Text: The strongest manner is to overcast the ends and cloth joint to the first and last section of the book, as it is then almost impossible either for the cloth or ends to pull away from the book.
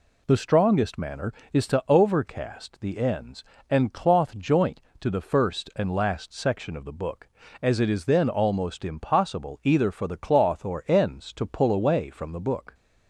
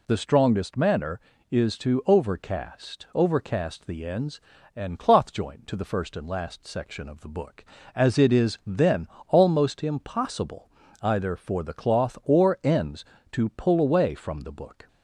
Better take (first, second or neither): first